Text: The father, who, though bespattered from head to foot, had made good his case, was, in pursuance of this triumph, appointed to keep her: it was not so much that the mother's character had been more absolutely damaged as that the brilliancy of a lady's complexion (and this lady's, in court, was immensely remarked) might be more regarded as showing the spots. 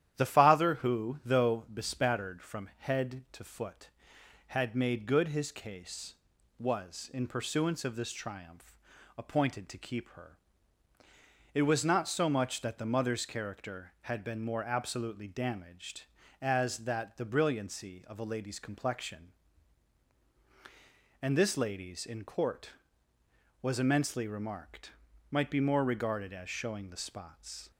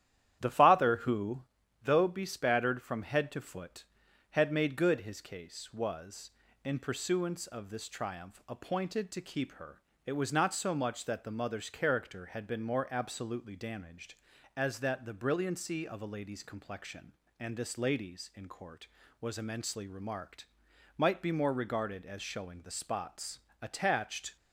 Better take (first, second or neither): first